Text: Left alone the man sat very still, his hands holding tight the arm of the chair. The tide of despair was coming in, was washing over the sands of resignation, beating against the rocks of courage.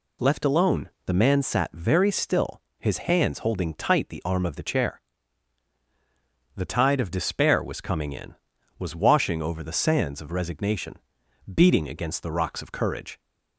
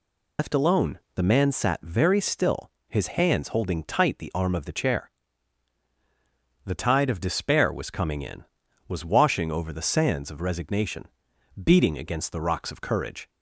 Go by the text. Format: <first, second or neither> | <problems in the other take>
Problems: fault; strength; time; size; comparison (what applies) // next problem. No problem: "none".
first | loses the start of "Left"; at 0.3 s; 100 ms // pauses between "alone" and "the"; slight; at 0.9 s; 0.16 s long; slight in the first